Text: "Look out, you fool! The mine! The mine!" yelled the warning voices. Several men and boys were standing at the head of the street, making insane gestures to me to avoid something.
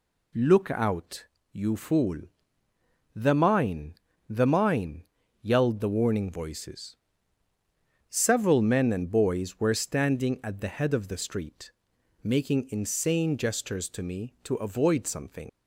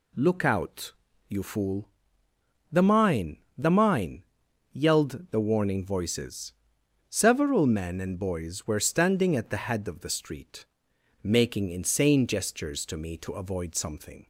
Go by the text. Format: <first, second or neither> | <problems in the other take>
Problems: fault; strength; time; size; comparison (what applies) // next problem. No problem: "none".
second | leaves "something" unfinished; at 15.4 s; 90 ms